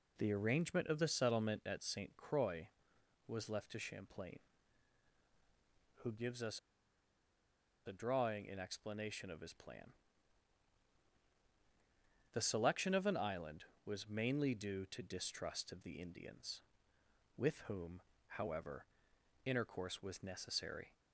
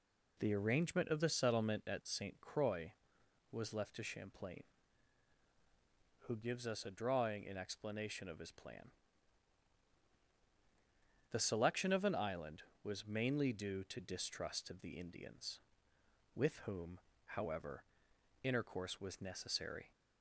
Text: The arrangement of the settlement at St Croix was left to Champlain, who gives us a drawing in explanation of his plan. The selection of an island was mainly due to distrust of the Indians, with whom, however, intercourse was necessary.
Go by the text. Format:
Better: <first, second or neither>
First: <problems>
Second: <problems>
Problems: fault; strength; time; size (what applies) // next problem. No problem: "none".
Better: second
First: pauses between "us" and "a"; strong; at 6.5 s; 1.2 s long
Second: none